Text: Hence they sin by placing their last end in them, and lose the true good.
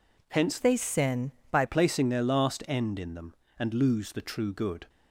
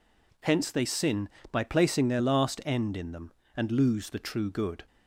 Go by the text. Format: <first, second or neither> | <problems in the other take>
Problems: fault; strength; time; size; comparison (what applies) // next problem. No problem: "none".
second | changes voice from "they" to "by"; from 0.5 to 1.6 s; 1.1 s long